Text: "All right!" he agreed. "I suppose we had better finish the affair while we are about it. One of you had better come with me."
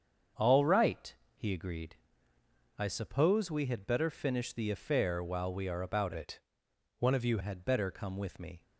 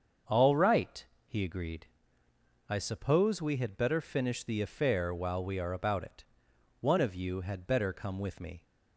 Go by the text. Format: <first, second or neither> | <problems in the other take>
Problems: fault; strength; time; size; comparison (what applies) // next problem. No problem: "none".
second | starts louder than the rest; strong; until 1.6 s; 7 dB; also in the second // changes voice from "it" to "you"; from 6.1 to 7.3 s; 1.2 s long